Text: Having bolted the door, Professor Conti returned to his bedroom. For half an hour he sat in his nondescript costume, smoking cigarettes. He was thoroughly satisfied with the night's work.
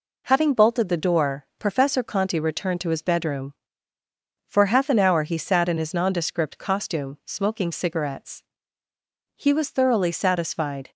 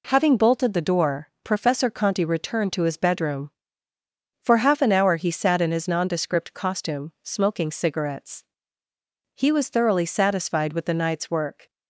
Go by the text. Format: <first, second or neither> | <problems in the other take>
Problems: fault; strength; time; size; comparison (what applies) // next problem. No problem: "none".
second | stops before "with the night's work"; at 10.9 s